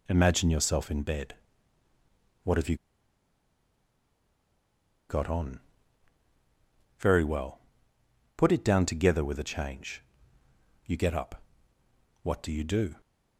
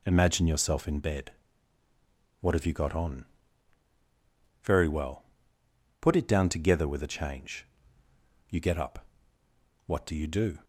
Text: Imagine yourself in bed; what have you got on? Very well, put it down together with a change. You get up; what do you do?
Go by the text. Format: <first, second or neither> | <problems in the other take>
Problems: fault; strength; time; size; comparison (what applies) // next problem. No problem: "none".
second | pauses between "you" and "got"; strong; at 2.7 s; 2.3 s long